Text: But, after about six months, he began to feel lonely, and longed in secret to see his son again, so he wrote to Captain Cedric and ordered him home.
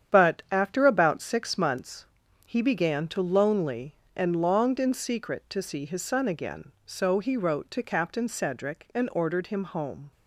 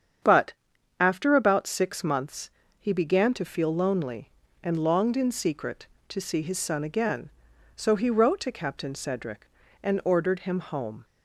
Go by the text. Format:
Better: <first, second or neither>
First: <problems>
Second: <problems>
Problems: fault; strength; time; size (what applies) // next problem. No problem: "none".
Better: second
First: starts louder than the rest; strong; until 1.2 s; 9 dB // skips "feel"; at 3.2 s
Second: starts louder than the rest; strong; until 1.7 s; 8 dB